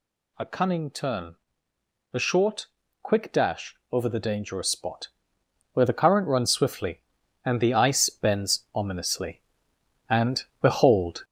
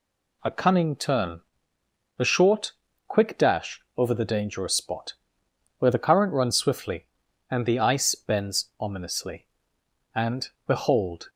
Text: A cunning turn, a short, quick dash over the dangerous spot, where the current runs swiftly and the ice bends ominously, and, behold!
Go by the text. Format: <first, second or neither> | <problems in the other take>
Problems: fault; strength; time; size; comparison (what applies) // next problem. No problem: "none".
second | gets louder; noticeable; throughout; 4.5 dB // pauses between "dash" and "over"; slight; at 3.7 s; 0.16 s long; slight in the second